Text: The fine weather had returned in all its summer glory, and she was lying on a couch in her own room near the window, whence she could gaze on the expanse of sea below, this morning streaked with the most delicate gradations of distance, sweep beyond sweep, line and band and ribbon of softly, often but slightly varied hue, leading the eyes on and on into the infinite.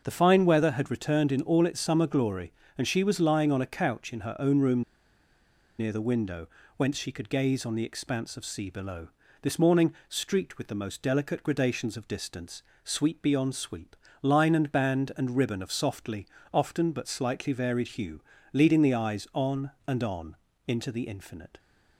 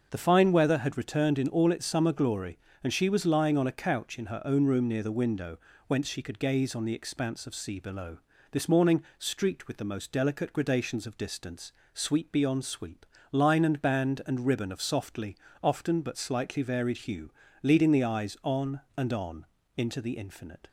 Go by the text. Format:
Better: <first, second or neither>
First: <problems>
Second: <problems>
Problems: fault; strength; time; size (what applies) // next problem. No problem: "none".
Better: second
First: starts louder than the rest; until 1.0 s; 6.5 dB // pauses between "room" and "near"; noticeable; at 4.8 s; 0.97 s long // pauses between "morning" and "streaked"; slight; at 9.9 s; 0.16 s long // pauses between "on" and "into"; slight; at 20.3 s; 0.32 s long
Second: starts louder than the rest; until 1.1 s; 6.5 dB // pauses between "morning" and "streaked"; slight; at 9.0 s; 0.16 s long // pauses between "on" and "into"; slight; at 19.4 s; 0.32 s long